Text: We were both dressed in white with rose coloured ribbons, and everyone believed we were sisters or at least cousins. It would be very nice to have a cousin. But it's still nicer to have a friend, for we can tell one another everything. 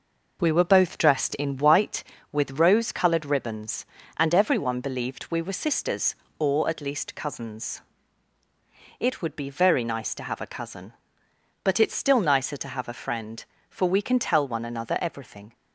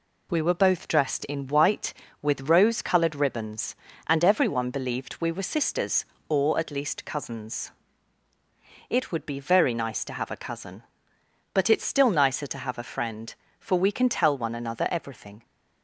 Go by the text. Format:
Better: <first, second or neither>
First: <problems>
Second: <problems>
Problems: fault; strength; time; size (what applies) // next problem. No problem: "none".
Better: second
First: starts louder than the rest; noticeable; until 1.8 s; 5 dB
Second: none